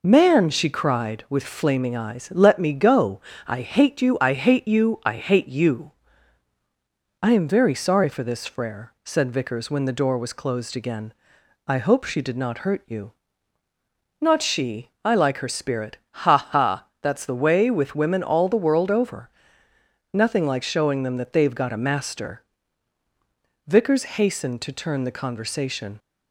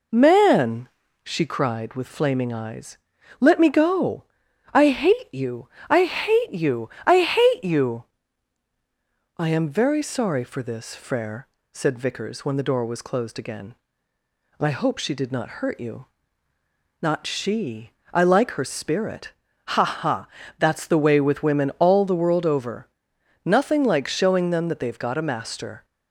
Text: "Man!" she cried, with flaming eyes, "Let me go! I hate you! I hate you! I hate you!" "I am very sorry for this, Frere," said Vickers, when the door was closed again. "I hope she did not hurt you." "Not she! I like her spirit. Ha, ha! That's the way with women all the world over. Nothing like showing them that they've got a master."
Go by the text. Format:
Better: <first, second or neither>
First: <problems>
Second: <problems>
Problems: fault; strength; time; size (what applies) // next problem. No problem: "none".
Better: second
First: goes on to say "Vickers hastened to turn the conversation"; strong; from 23.6 s on; 2.3 s long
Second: none